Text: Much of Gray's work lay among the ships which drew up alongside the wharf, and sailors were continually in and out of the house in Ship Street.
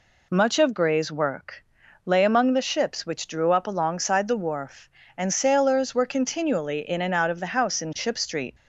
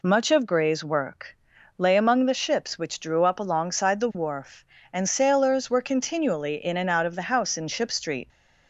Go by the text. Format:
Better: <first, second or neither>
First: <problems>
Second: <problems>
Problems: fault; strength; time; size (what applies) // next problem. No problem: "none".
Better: neither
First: pauses between "work" and "lay"; noticeable; at 1.5 s; 0.50 s long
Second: pauses between "work" and "lay"; noticeable; at 1.2 s; 0.50 s long